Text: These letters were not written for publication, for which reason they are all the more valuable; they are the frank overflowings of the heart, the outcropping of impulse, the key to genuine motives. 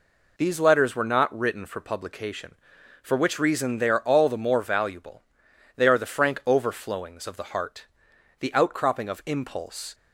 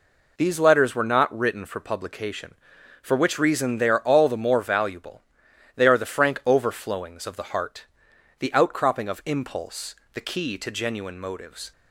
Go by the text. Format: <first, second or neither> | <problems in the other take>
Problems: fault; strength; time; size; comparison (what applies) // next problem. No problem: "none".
second | stops before "the key to genuine motives"; at 9.9 s